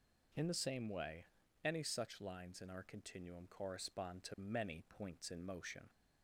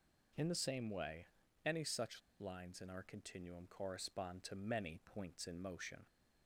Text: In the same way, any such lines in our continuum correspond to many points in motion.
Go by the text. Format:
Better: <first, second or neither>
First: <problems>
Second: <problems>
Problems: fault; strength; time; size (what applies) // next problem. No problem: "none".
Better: first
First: none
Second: pauses between "such" and "lines"; slight; at 2.2 s; 0.19 s long